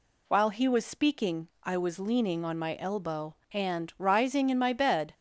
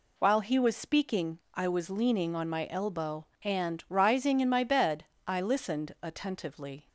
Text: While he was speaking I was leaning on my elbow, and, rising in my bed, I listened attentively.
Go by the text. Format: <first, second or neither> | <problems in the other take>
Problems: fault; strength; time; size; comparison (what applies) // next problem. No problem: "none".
second | stops before "I listened attentively"; at 5.1 s